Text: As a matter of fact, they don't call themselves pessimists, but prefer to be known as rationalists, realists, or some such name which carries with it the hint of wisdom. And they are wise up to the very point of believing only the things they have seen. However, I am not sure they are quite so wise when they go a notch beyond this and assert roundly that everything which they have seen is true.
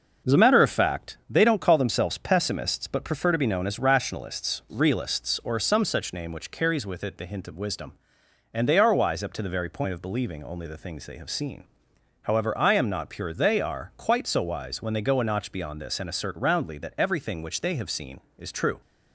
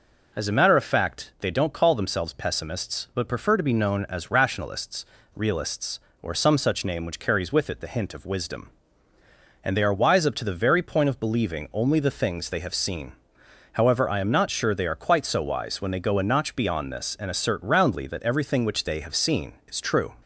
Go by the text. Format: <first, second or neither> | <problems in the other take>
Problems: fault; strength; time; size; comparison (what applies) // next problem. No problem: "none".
second | says "pure" for "sure"; at 13.0 s